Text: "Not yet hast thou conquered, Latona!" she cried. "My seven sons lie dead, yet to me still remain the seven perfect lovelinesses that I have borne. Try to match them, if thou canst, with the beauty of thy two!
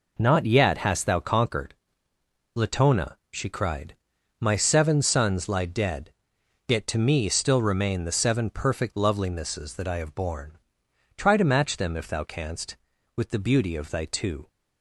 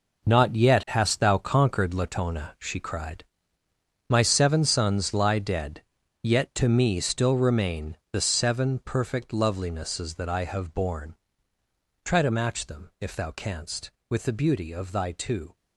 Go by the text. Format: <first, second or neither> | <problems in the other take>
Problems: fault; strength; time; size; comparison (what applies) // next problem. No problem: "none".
first | gets quieter; strong; throughout; 10.5 dB // pauses between "remain" and "the"; slight; at 7.9 s; 0.16 s long